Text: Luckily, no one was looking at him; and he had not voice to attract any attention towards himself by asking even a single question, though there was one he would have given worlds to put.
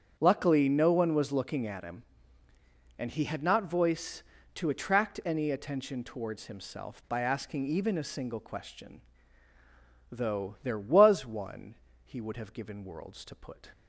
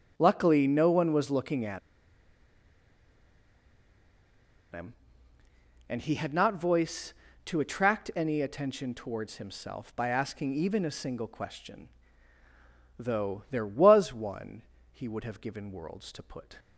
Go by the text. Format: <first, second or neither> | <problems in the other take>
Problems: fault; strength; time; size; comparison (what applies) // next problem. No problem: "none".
first | starts louder than the rest; strong; until 1.1 s; 7.5 dB; strong in the first // pauses between "at" and "him"; strong; at 1.7 s; 2.9 s long // pauses between "one" and "he"; slight; at 14.6 s; 0.30 s long; slight in the first